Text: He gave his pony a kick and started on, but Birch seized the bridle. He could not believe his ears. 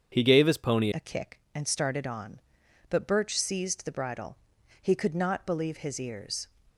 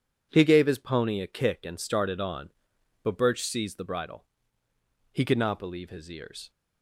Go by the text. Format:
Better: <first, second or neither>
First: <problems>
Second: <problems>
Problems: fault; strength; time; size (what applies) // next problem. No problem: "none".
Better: second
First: starts louder than the rest; strong; until 1.1 s; 7.5 dB // changes voice at "a"; from 0.9 s on; 5.5 s long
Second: none